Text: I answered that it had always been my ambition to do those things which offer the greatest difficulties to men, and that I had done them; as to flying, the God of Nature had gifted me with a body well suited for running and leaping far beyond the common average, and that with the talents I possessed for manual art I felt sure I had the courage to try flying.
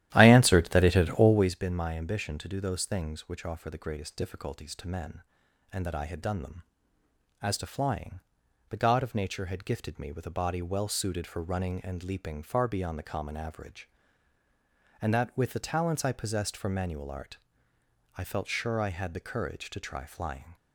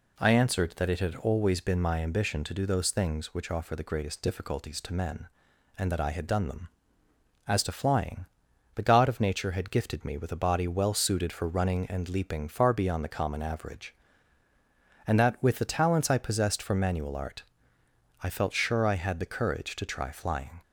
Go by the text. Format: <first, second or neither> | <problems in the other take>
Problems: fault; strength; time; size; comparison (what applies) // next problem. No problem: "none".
second | starts louder than the rest; strong; until 1.6 s; 13 dB // pauses between "art" and "I"; noticeable; at 17.3 s; 0.80 s long; noticeable in the second